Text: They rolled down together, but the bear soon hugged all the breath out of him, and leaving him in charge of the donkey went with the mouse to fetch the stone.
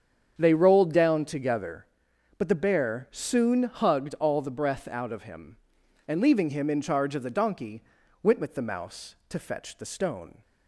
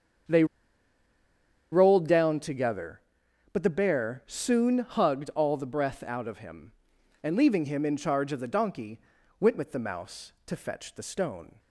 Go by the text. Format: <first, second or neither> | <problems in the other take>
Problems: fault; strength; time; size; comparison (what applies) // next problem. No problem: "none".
first | starts louder than the rest; strong; until 2.5 s; 8 dB; strong in the first // pauses between "They" and "rolled"; strong; at 0.4 s; 1.2 s long // pauses between "donkey" and "went"; at 8.9 s; 0.40 s long; also in the first